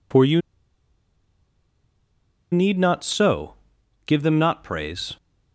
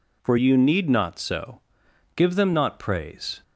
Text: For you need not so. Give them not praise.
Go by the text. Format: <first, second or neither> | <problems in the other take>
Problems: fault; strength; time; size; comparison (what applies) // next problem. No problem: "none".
second | pauses between "you" and "need"; strong; at 0.4 s; 2.1 s long